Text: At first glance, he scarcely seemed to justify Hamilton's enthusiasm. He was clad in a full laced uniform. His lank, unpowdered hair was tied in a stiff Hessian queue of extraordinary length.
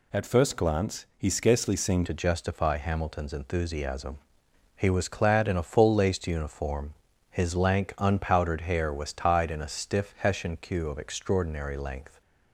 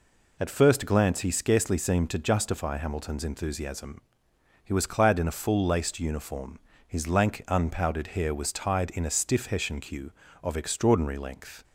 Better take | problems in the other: second | changes voice at "to"; from 2.0 s on; 10.2 s long

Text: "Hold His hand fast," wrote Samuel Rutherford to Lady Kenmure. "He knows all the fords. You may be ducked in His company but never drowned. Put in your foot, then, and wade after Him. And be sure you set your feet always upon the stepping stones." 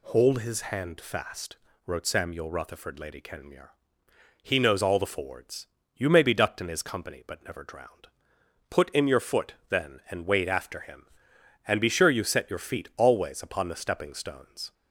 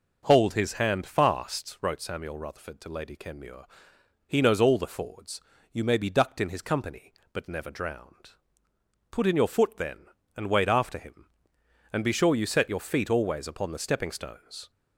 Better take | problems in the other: second | skips "to"; at 2.9 s

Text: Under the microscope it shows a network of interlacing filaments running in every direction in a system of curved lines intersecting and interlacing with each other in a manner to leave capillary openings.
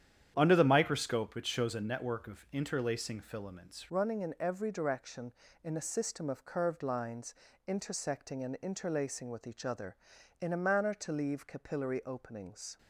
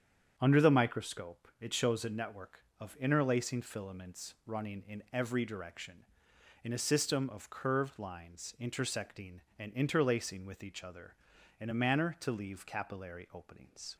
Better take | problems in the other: second | starts louder than the rest; strong; until 1.3 s; 9.5 dB; strong in the second // changes voice at "running"; from 3.8 s on; 8.9 s long // pauses between "lines" and "intersecting"; slight; at 7.3 s; 0.32 s long

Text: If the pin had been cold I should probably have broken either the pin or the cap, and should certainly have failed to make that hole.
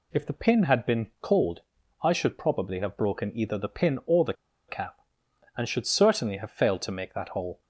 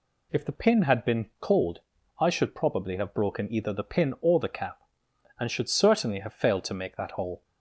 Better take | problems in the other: second | pauses between "cold" and "I"; at 1.6 s; 0.42 s long; also in the second // pauses between "the" and "cap"; slight; at 4.3 s; 0.35 s long

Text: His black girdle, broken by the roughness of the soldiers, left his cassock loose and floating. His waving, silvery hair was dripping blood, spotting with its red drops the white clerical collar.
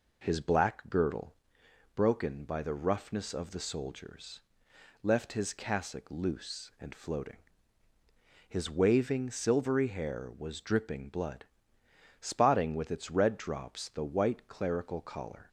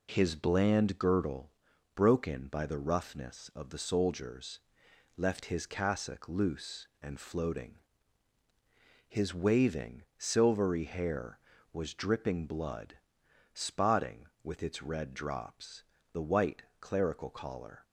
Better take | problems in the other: first | says "bland" for "black"; at 0.3 s // pauses between "drops" and "the"; slight; at 15.8 s; 0.28 s long // pauses between "white" and "clerical"; slight; at 16.6 s; 0.16 s long

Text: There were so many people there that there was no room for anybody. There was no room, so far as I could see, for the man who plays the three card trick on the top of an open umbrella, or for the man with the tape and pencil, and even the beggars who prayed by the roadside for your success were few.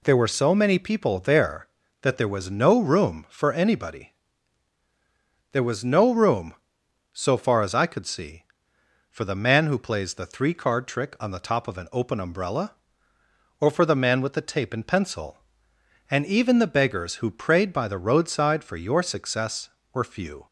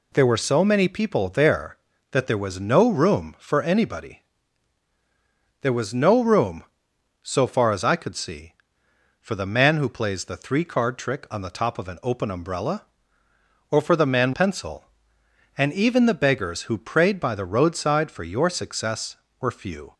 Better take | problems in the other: first | skips "with the tape and"; at 14.3 s

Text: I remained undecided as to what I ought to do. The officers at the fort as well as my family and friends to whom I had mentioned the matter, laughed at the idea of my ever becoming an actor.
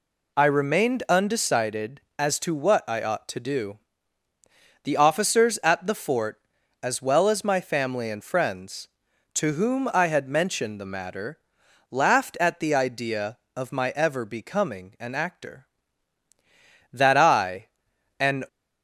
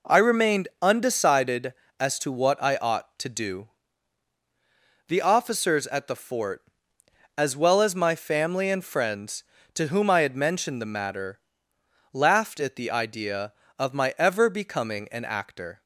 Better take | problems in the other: second | goes on to say "That I an"; from 16.9 s on; 1.5 s long

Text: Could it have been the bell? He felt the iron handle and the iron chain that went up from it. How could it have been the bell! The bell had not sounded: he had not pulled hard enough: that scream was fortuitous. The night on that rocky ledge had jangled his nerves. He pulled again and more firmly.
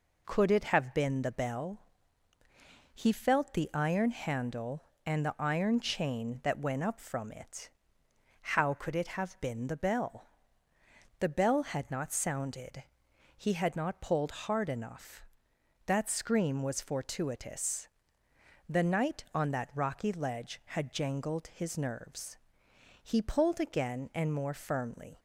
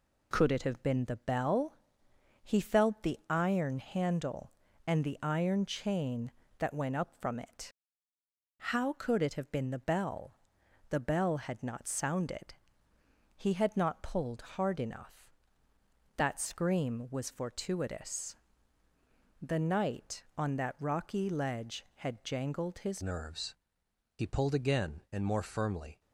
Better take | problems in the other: first | pauses between "pulled" and "hard"; slight; at 14.3 s; 0.16 s long // changes voice at "nerves"; from 23.0 s on; 2.9 s long

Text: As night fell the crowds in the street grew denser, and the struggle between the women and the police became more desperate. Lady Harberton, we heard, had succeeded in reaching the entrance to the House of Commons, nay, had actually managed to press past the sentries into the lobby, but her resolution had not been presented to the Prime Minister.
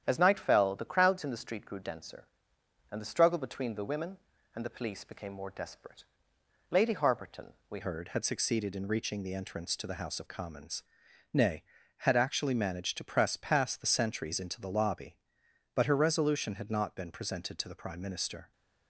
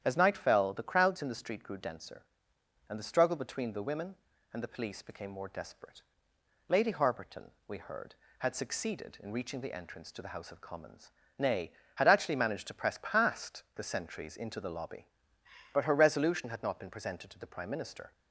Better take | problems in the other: second | starts louder than the rest; strong; until 1.0 s; 9.5 dB; strong in the second // changes voice at "heard"; from 7.8 s on; 10.7 s long

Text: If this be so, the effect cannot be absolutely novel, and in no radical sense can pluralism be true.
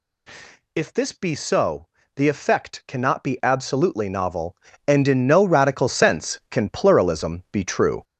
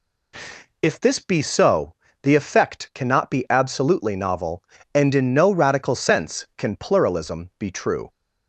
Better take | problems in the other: second | gets louder; throughout; 6.5 dB

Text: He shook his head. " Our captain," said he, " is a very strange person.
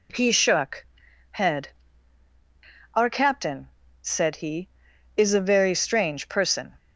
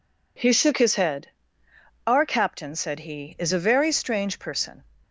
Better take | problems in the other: second | skips "his"; at 1.0 s

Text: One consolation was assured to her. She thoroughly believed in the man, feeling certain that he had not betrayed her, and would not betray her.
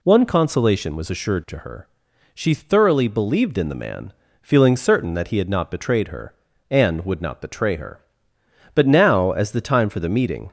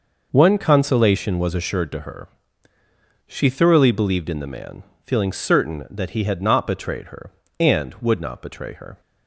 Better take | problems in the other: second | goes on to say "But now as the time for the meeting"; strong; from 8.7 s on; 1.7 s long

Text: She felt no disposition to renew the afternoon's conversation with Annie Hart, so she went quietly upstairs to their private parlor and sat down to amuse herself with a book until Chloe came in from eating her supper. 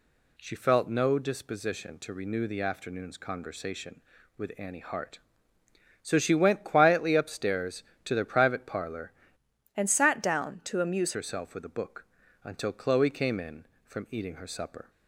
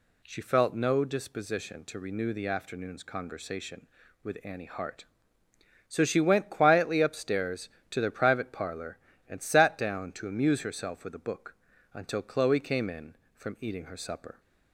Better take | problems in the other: second | changes voice from "and" to "amuse"; from 9.7 to 11.1 s; 1.4 s long // pauses between "book" and "until"; at 12.0 s; 0.40 s long; also in the second

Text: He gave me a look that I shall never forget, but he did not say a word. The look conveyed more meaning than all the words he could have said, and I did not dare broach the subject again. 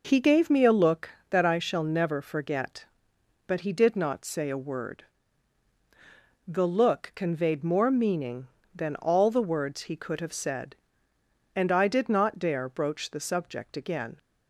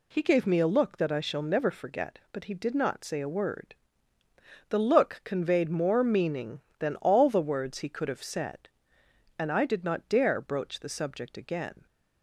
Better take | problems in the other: neither | none

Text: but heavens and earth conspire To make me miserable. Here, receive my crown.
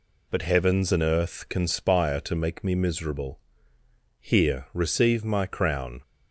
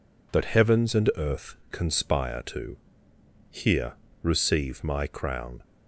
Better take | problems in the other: first | pauses between "earth" and "conspire"; slight; at 1.5 s; 0.16 s long // skips "make me miserable"; at 3.1 s

